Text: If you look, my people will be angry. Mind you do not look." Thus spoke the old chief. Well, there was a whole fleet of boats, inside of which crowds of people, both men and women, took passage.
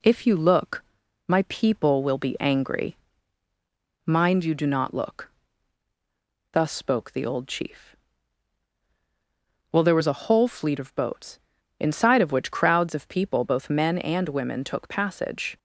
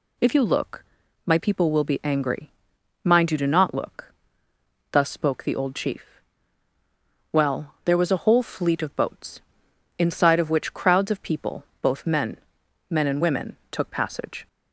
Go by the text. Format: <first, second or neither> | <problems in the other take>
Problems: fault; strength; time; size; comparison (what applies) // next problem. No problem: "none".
first | says "men" twice; at 12.8 s